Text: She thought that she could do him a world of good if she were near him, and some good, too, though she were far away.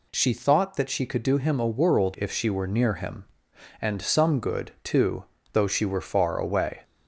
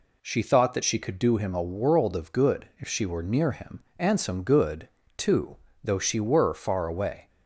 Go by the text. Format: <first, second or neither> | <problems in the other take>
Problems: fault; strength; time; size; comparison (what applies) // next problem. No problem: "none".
second | skips "of good"; at 2.1 s